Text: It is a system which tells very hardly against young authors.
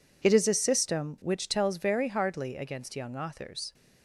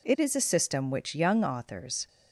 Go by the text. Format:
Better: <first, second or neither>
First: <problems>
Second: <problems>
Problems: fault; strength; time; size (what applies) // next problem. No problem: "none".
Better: first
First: none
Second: skips "tells very hardly against"; at 1.1 s